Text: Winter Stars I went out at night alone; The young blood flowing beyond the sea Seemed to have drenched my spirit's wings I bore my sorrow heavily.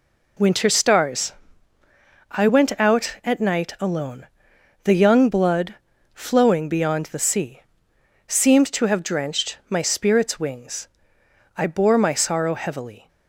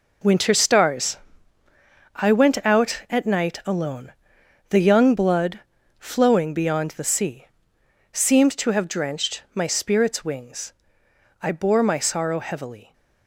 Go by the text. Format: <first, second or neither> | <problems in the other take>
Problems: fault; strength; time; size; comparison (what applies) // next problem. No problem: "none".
first | gets quieter; strong; throughout; 9.5 dB // pauses between "Stars" and "I"; noticeable; at 1.1 s; 0.98 s long; noticeable in the first // pauses between "blood" and "flowing"; at 5.6 s; 0.38 s long; also in the first // pauses between "sea" and "Seemed"; noticeable; at 7.4 s; 0.66 s long; noticeable in the first // pauses between "wings" and "I"; noticeable; at 10.7 s; 0.66 s long; noticeable in the first